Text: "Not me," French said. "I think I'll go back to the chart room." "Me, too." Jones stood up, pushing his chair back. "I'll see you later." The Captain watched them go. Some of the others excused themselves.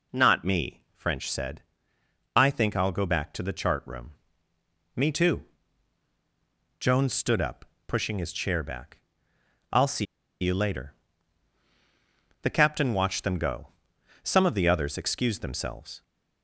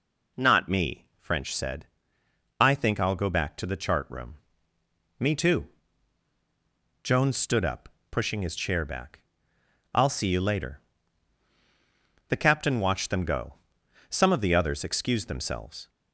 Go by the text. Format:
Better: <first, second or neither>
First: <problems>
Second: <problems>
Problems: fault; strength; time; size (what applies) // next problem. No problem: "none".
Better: second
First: pauses between "see" and "you"; slight; at 10.0 s; 0.35 s long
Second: none